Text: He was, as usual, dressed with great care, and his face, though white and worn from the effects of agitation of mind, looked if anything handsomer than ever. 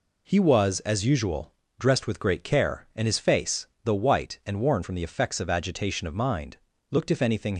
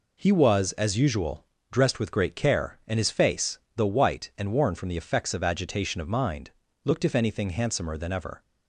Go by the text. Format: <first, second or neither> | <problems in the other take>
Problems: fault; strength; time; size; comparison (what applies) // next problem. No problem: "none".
second | stops before "handsomer than ever"; at 7.5 s